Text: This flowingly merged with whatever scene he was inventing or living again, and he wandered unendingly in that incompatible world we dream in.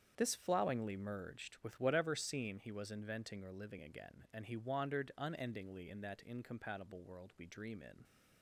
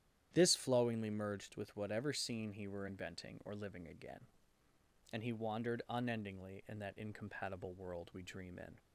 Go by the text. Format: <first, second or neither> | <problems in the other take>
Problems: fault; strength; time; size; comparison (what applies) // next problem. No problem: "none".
first | starts louder than the rest; strong; until 1.3 s; 11.5 dB; strong in the first // says "were" for "was"; at 2.6 s